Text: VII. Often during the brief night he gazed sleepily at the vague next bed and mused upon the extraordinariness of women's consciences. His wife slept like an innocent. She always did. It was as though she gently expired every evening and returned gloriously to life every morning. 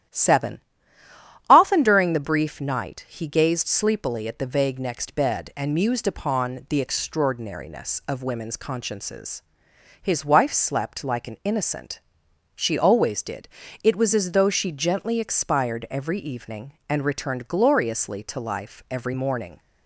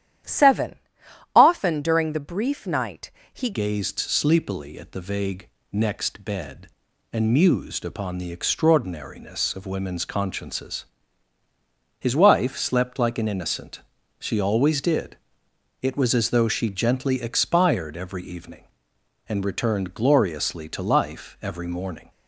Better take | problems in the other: first | starts louder than the rest; strong; until 1.8 s; 11 dB; strong in the first // pauses between "night" and "he"; slight; at 3.1 s; 0.20 s long // changes voice at "gazed"; from 3.5 s on; 18.6 s long // pauses between "vague" and "next"; slight; at 5.4 s; 0.26 s long

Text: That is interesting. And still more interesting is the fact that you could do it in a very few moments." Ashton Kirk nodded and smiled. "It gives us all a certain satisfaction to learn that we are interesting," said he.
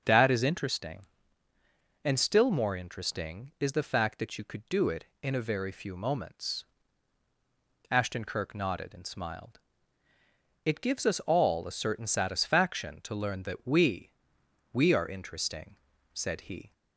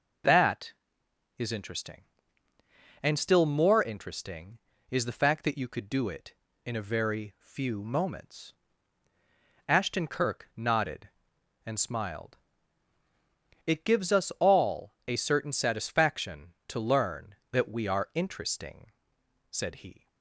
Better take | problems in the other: second | starts louder than the rest; until 1.0 s; 6 dB // says "we" twice; at 14.7 s

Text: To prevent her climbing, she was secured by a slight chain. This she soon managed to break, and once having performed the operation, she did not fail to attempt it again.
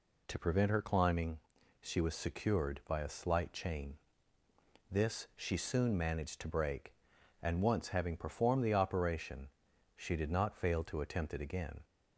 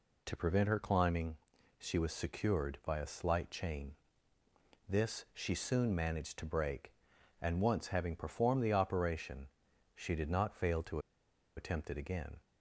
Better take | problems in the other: first | pauses between "to" and "attempt"; noticeable; at 10.9 s; 0.57 s long

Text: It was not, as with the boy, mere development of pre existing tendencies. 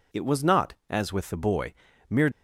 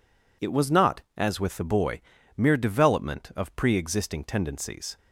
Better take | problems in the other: second | stops before "development of pre existing tendencies"; at 2.3 s

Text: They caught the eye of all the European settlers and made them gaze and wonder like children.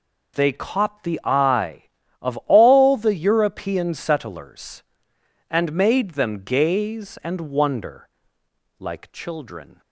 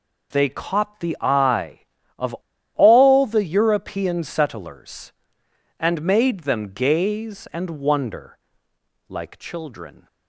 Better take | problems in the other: first | pauses between "of" and "all"; at 2.3 s; 0.42 s long // pauses between "wonder" and "like"; noticeable; at 8.3 s; 0.72 s long; noticeable in the first

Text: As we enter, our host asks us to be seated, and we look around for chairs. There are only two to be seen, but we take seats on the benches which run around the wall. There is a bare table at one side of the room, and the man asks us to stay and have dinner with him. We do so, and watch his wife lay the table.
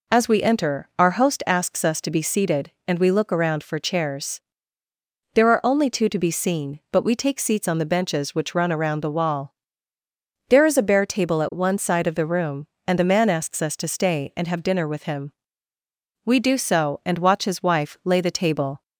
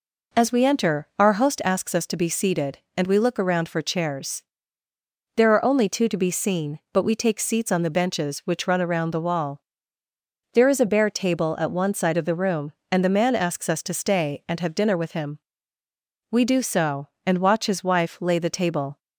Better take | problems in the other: neither | none

